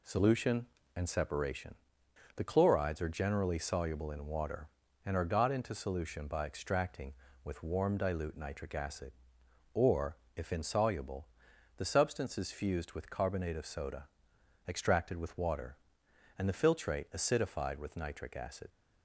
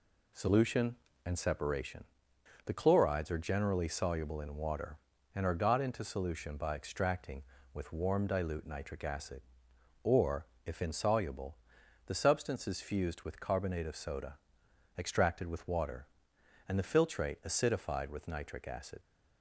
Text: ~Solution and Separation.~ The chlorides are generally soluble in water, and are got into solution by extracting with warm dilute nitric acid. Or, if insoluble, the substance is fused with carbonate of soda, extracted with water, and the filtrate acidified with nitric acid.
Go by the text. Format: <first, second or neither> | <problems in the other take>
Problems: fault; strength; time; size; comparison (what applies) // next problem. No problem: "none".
neither | none